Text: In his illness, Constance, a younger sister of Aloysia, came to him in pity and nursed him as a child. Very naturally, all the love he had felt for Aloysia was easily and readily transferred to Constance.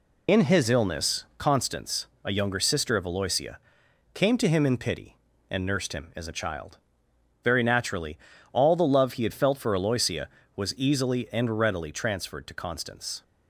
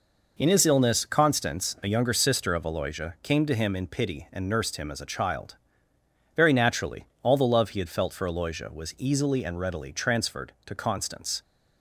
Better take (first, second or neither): second